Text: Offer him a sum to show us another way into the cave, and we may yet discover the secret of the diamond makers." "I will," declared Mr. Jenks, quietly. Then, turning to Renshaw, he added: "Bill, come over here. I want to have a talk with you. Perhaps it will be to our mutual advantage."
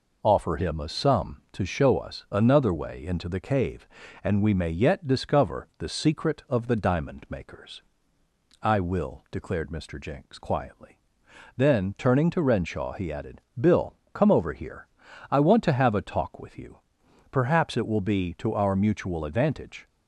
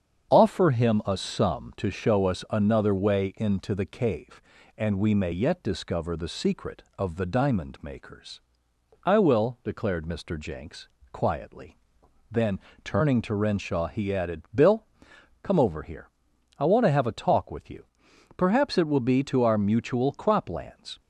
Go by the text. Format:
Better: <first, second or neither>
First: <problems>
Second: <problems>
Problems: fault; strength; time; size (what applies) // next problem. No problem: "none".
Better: first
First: none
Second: starts louder than the rest; strong; until 1.3 s; 7.5 dB // says "croplands" for "advantage"; at 20.1 s